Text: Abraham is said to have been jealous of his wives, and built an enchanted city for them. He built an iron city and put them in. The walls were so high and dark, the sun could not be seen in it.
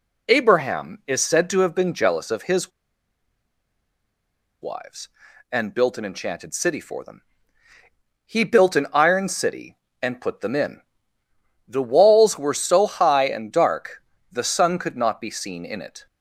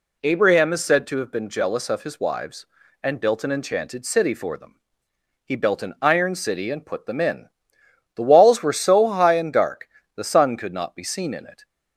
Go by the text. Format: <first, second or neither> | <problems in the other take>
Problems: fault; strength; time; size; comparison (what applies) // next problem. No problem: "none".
second | pauses between "his" and "wives"; strong; at 2.7 s; 1.9 s long